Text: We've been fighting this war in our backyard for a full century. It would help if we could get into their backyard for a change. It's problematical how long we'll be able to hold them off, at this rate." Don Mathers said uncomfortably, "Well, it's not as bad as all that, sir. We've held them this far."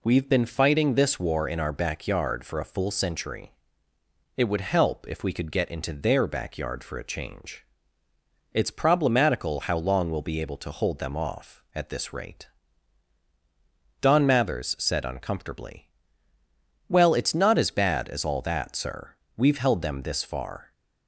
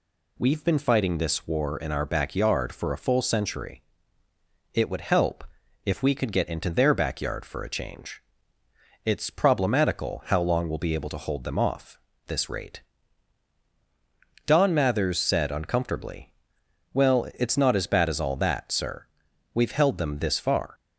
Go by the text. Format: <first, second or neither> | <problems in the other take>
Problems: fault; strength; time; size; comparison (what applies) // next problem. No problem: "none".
first | pauses between "help" and "if"; at 5.4 s; 0.42 s long // skips "at"; at 12.1 s